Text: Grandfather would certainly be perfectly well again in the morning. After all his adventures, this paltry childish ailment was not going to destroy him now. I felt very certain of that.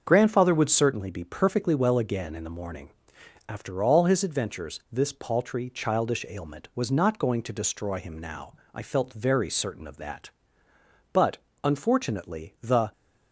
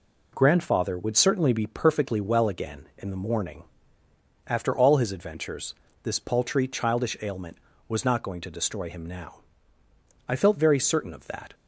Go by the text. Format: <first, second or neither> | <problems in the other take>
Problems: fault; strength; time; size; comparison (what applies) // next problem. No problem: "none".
second | starts louder than the rest; until 1.0 s; 6.5 dB // goes on to say "But unfortunately the"; strong; from 11.1 s on; 1.8 s long